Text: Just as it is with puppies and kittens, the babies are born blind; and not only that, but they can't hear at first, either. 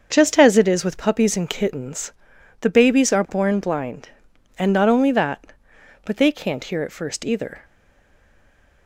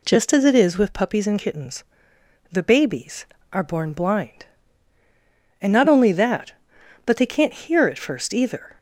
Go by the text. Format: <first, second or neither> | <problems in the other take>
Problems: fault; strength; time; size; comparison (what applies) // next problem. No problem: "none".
second | starts louder than the rest; until 1.1 s; 6.5 dB // stays silent after the last word; noticeable; from 7.6 s on; 1.2 s long